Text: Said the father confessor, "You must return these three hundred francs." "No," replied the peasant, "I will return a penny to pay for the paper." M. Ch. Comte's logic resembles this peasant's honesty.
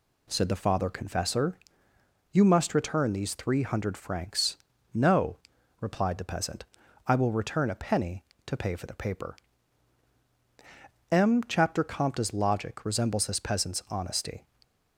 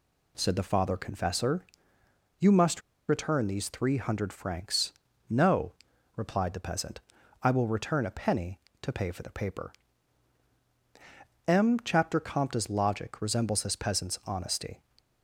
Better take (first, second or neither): first